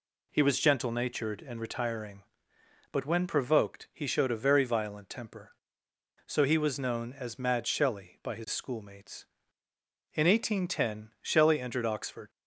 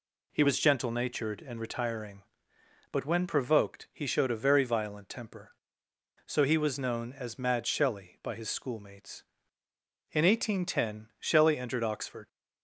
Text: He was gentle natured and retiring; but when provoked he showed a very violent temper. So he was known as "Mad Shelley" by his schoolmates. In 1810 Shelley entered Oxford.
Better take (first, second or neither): neither